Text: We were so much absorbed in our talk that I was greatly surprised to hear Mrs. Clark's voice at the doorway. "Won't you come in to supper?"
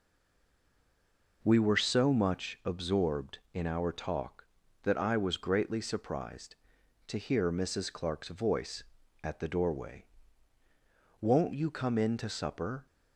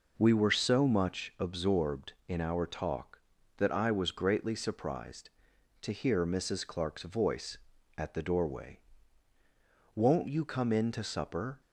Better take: second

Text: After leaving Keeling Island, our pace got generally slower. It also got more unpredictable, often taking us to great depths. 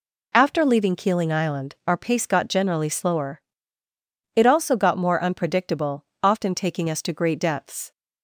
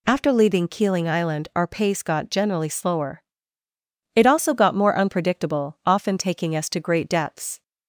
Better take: neither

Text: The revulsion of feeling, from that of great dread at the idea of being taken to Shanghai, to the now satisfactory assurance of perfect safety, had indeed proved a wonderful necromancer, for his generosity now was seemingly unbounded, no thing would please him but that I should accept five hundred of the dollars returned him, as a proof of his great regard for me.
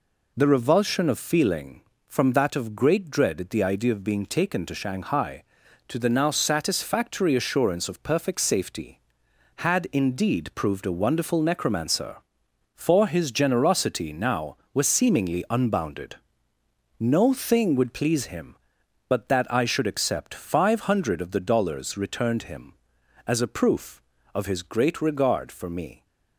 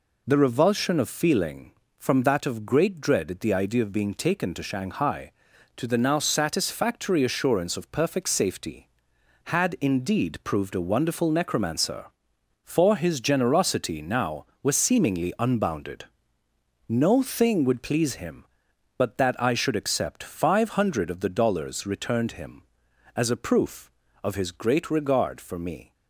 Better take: neither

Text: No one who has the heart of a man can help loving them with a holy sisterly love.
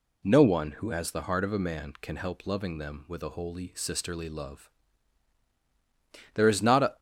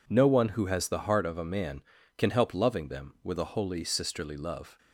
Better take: second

